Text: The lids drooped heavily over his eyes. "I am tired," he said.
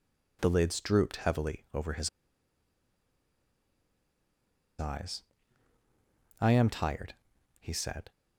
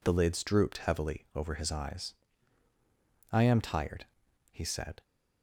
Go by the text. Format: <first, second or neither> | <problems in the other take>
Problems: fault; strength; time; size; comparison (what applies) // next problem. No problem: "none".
second | pauses between "his" and "eyes"; strong; at 2.0 s; 2.7 s long